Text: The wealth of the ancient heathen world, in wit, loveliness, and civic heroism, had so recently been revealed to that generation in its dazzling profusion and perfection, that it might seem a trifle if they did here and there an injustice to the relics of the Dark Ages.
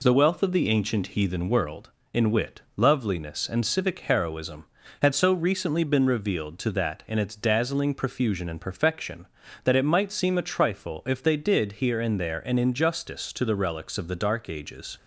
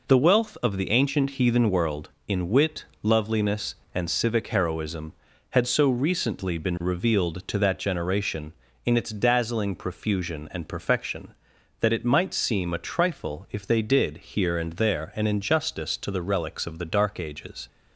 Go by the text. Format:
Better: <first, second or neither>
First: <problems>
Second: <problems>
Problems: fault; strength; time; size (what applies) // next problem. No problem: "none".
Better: second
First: skips "generation"; at 7.0 s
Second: none